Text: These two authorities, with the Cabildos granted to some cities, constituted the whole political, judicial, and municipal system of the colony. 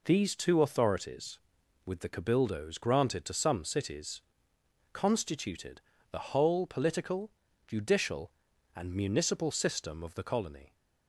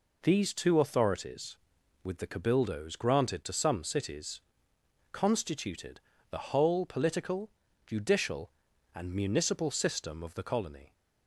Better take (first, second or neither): neither